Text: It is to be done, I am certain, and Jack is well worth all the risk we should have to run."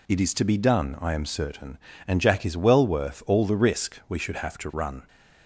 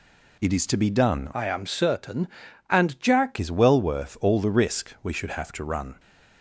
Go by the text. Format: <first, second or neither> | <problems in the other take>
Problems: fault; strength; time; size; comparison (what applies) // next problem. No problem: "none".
first | changes voice from "I" to "Jack"; from 1.3 to 3.3 s; 2.0 s long